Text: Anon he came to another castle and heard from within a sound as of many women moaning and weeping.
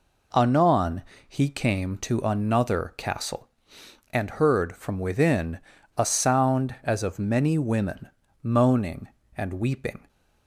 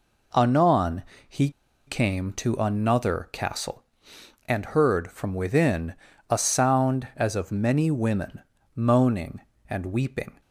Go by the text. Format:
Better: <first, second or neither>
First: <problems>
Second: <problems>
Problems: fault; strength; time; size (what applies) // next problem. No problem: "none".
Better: first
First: pauses between "Anon" and "he"; slight; at 1.0 s; 0.24 s long // pauses between "within" and "a"; at 5.5 s; 0.36 s long // pauses between "women" and "moaning"; slight; at 8.0 s; 0.34 s long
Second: pauses between "Anon" and "he"; slight; at 1.0 s; 0.24 s long // pauses between "he" and "came"; at 1.4 s; 0.37 s long // pauses between "within" and "a"; slight; at 5.9 s; 0.34 s long // pauses between "women" and "moaning"; slight; at 8.4 s; 0.34 s long